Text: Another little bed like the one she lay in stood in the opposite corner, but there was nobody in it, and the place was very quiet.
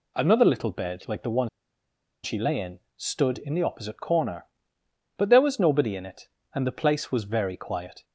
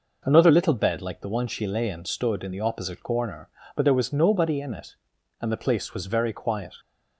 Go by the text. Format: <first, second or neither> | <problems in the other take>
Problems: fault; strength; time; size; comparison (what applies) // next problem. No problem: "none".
second | pauses between "one" and "she"; noticeable; at 1.4 s; 0.75 s long // pauses between "in" and "stood"; slight; at 2.7 s; 0.18 s long